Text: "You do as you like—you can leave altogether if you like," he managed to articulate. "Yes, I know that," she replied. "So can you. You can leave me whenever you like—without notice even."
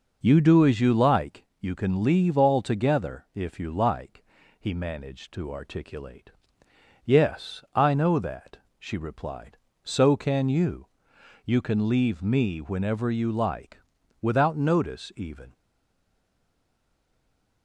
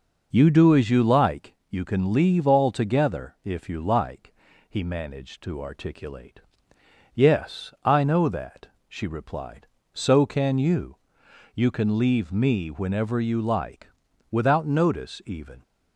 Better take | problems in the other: second | stays silent after the last word; from 15.5 s on; 2.1 s long

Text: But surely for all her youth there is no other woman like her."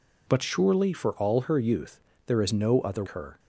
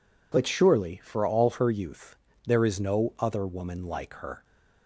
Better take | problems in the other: second | pauses between "youth" and "there"; slight; at 1.9 s; 0.26 s long; slight in the second // skips "woman like"; at 3.0 s

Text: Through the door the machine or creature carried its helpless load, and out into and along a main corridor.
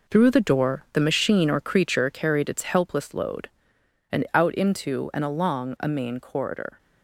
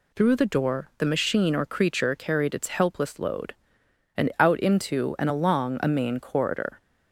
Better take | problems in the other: second | gets quieter; strong; throughout; 7.5 dB

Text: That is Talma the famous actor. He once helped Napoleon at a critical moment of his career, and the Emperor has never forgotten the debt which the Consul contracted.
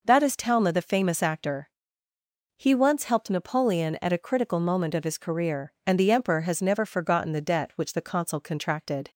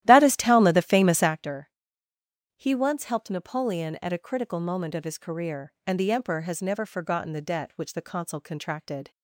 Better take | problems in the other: first | starts louder than the rest; strong; until 1.4 s; 13.5 dB

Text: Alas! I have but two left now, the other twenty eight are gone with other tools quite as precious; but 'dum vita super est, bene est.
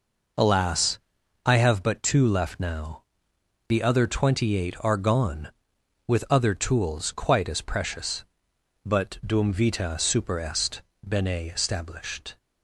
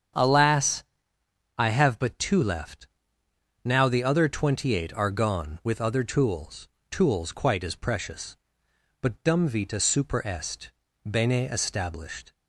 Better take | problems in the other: first | starts louder than the rest; strong; until 1.9 s; 8.5 dB // pauses between "left" and "now"; noticeable; at 2.8 s; 0.78 s long // says "tools" twice; at 6.8 s

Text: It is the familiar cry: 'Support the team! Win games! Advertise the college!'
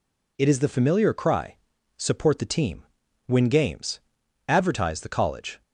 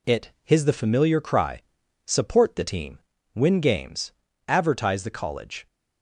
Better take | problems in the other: first | says "his" for "is"; at 0.4 s

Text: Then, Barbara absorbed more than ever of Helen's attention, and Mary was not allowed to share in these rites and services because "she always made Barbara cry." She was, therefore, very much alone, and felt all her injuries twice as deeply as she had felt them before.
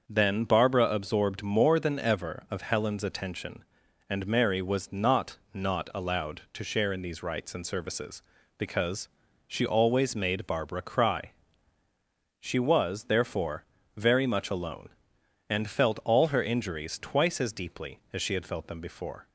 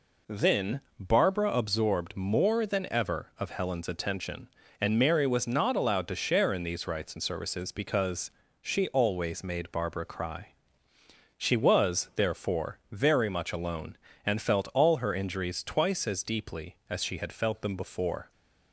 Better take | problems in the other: second | starts louder than the rest; until 1.0 s; 6.5 dB // says "not" twice; at 5.5 s // pauses between "because" and "she"; at 9.0 s; 0.38 s long; slight in the second

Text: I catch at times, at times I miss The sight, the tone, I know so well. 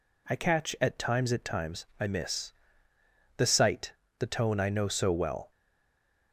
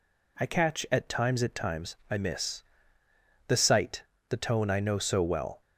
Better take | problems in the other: second | pauses between "miss" and "The"; noticeable; at 2.5 s; 0.86 s long; noticeable in the second // stays silent after the last word; slight; from 5.5 s on; 0.8 s long

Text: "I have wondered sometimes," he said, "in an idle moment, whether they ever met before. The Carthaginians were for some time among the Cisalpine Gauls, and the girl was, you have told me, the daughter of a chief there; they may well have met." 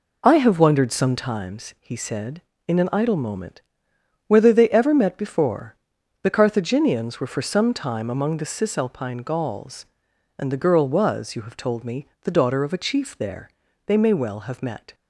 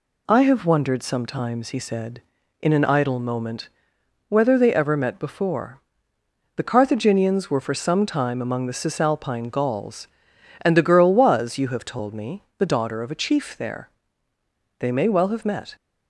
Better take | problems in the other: second | starts louder than the rest; until 1.5 s; 4 dB

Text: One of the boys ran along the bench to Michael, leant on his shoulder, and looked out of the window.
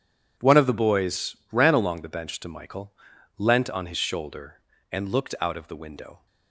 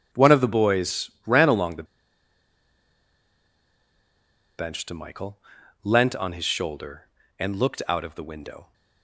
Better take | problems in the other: first | pauses between "boys" and "ran"; slight; at 1.0 s; 0.16 s long; slight in the first // pauses between "the" and "bench"; strong; at 1.8 s; 2.7 s long

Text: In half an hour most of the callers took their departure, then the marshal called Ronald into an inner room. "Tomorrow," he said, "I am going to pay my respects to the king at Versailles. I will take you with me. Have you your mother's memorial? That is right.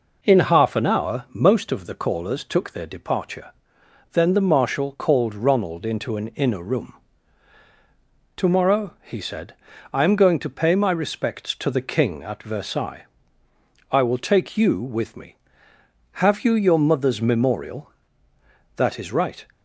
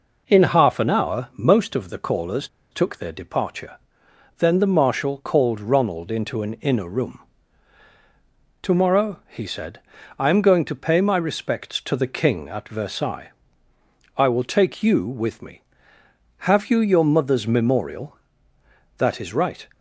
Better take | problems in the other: first | pauses between "callers" and "took"; slight; at 2.4 s; 0.24 s long

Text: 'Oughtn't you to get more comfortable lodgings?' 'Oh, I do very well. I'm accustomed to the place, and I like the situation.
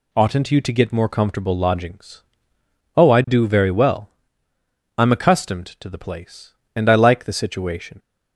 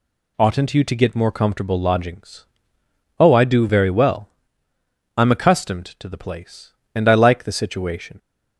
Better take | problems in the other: neither | none

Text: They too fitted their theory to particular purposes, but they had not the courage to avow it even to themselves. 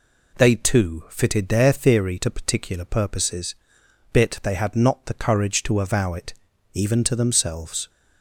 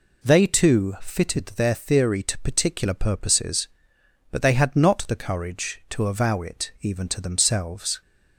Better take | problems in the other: second | says "bit" for "but"; at 4.1 s // pauses between "it" and "even"; at 6.3 s; 0.40 s long

